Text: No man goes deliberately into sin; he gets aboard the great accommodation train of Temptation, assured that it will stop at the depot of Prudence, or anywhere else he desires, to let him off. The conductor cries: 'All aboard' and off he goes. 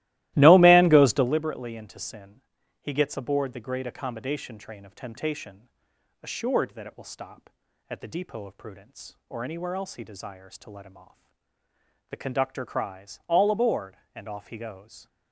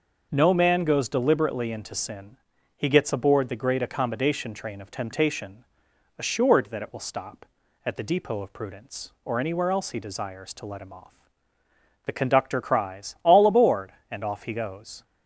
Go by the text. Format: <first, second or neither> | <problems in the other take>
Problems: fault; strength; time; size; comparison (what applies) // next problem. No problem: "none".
second | starts louder than the rest; strong; until 1.4 s; 17 dB